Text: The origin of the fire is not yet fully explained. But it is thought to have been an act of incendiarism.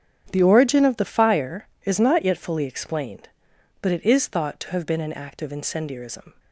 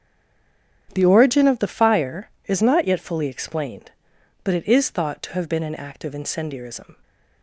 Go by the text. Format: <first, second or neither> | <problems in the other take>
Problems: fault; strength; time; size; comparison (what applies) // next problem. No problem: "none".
first | stays silent before the first word; slight; until 0.8 s; 0.8 s long // starts louder than the rest; strong; until 1.9 s; 9 dB; strong in the first